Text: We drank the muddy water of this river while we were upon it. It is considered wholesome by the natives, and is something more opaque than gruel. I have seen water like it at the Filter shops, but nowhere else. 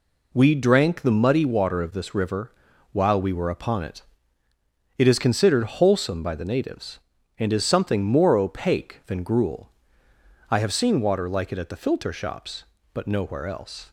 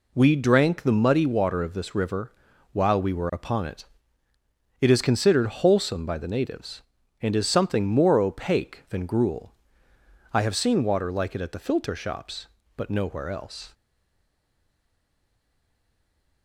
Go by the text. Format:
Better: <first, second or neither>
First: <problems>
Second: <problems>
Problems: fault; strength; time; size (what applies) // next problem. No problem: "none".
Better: first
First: pauses between "river" and "while"; at 2.5 s; 0.40 s long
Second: pauses between "river" and "while"; at 2.3 s; 0.40 s long // stays silent after the last word; strong; from 13.7 s on; 2.7 s long